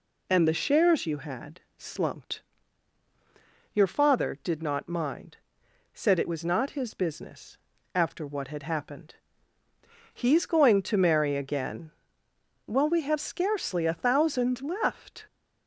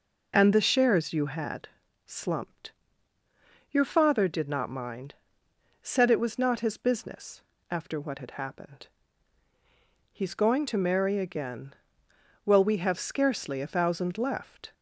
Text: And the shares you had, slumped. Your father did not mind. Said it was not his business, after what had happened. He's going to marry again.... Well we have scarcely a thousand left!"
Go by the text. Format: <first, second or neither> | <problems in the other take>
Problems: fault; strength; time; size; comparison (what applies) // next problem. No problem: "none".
neither | none